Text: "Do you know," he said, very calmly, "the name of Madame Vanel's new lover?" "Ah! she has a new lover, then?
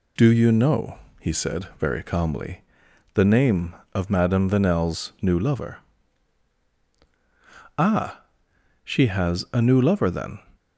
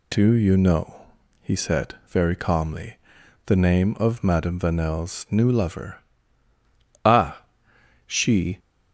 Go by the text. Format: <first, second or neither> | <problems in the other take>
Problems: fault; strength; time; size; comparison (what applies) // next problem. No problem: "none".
first | stops before "has a new lover then"; at 8.5 s